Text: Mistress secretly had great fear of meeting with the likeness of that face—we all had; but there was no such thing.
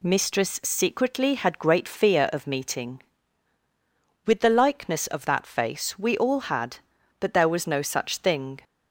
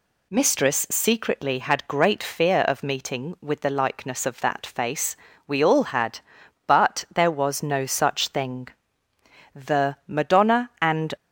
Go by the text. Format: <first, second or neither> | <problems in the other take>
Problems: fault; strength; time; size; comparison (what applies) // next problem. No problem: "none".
first | goes on to say "The Madonna and"; from 9.5 s on; 1.6 s long